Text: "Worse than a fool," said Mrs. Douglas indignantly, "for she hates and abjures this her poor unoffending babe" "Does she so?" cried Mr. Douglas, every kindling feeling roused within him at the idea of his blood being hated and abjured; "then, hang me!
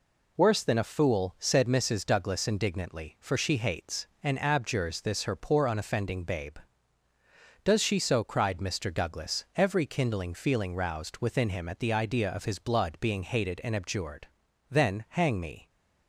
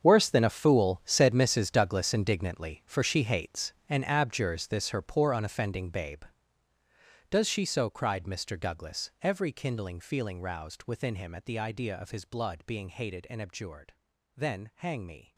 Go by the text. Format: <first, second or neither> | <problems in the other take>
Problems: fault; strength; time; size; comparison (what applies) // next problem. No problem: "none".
first | gets quieter; strong; throughout; 15.5 dB